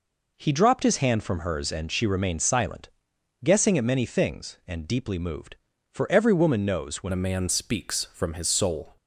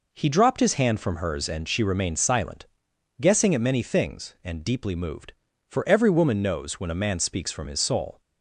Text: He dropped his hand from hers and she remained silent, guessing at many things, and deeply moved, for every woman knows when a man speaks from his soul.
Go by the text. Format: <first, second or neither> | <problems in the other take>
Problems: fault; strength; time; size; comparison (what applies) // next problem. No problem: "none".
second | changes voice at "a"; from 7.1 s on; 1.8 s long